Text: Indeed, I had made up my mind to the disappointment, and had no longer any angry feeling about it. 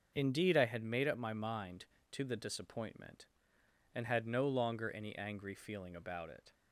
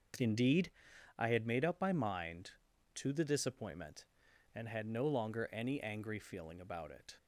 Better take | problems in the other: neither | starts louder than the rest; the same in both

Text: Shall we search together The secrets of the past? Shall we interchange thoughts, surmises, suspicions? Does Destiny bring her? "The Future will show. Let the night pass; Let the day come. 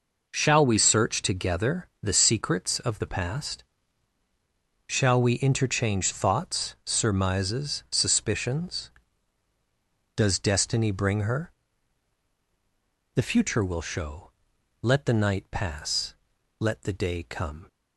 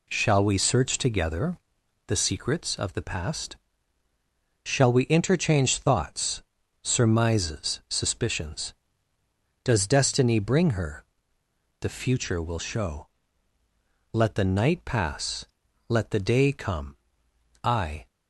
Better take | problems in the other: first | pauses between "together" and "The"; noticeable; at 1.5 s; 0.50 s long // goes on to say "I"; slight; from 17.6 s on; 0.42 s long

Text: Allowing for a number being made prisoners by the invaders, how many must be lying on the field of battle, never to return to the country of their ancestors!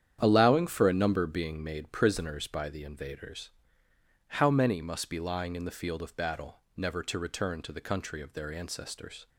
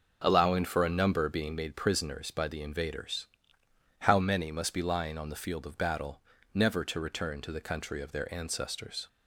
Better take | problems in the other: second | starts louder than the rest; strong; until 1.2 s; 9 dB; noticeable in the second // says "in" for "on"; at 5.5 s

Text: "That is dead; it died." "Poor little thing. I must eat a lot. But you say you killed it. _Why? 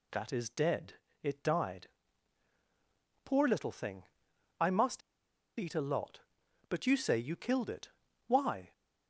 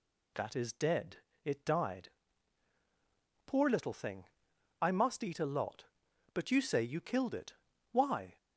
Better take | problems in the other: second | pauses between "must" and "eat"; noticeable; at 5.0 s; 0.59 s long

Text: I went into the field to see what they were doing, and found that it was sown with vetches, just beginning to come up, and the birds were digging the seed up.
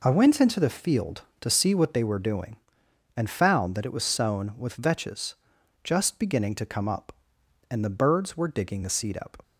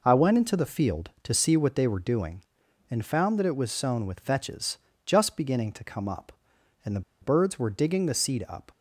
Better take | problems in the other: first | pauses between "the" and "birds"; slight; at 7.0 s; 0.21 s long

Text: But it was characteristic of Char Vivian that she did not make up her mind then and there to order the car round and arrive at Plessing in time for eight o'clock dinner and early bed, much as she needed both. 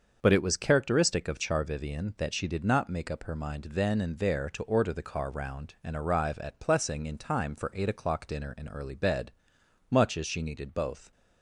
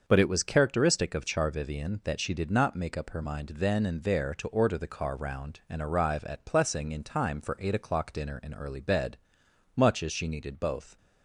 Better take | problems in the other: neither | starts louder than the rest; the same in both

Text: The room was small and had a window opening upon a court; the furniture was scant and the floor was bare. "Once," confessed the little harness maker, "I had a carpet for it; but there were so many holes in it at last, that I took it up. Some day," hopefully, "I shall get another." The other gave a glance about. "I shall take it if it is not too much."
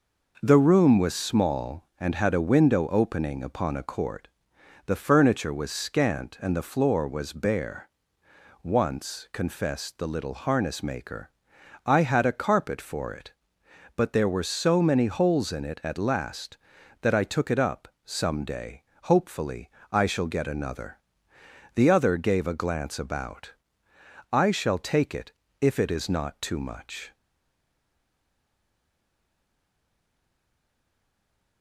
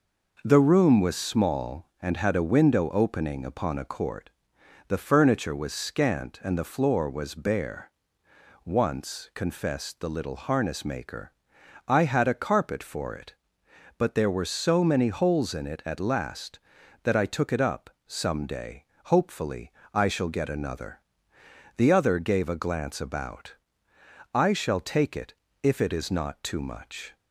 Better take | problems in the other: second | pauses between "it" and "if"; slight; at 25.3 s; 0.30 s long; slight in the second // stays silent after the last word; strong; from 27.1 s on; 4.5 s long

